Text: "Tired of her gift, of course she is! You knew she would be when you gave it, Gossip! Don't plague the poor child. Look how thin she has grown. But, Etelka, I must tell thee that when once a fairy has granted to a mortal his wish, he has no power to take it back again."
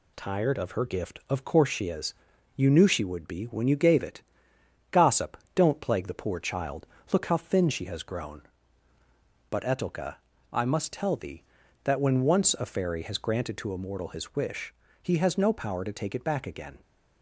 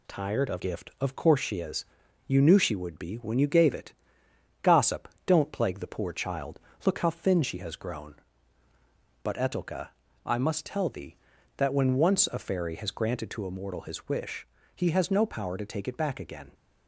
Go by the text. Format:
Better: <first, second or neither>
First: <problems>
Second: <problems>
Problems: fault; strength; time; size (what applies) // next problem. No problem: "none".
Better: first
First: none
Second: skips "her"; at 0.5 s